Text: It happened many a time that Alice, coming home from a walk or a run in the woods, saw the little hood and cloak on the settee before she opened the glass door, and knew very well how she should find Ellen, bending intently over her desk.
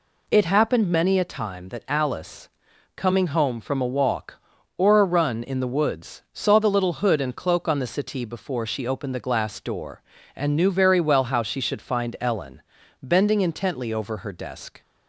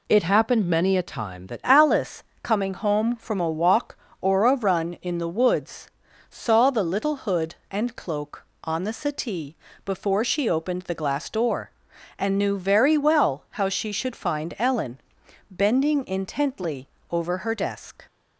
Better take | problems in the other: first | changes voice at "Alice"; from 1.6 s on; 16.4 s long // pauses between "settee" and "before"; slight; at 9.5 s; 0.30 s long // pauses between "intently" and "over"; slight; at 16.8 s; 0.24 s long

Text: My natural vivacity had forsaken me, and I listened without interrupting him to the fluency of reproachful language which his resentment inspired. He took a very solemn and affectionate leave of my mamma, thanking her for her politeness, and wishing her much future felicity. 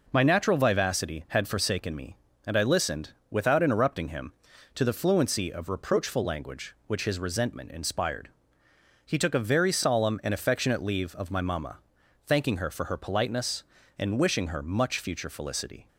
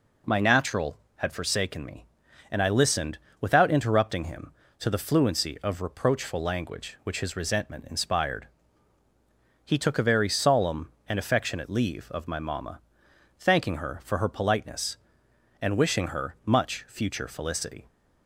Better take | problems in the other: first | skips "vivacity"; at 1.0 s // pauses between "listened" and "without"; slight; at 3.1 s; 0.22 s long; slight in the first

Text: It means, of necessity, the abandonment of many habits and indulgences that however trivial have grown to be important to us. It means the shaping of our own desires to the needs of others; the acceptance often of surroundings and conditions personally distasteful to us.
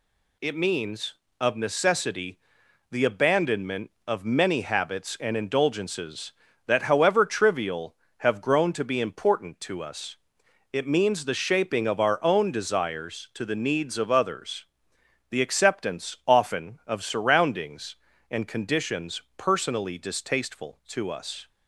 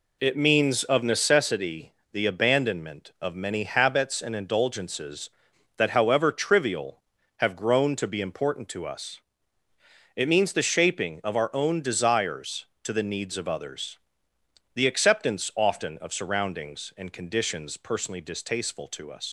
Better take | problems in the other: first | leaves "us" unfinished; at 19.2 s; 85 ms

